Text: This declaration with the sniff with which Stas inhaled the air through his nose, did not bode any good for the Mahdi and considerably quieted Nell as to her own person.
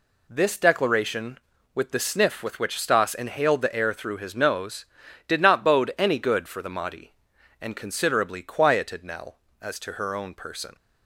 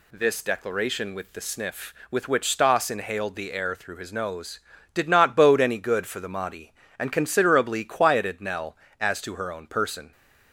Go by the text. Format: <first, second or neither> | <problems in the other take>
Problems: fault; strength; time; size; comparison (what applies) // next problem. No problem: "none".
neither | none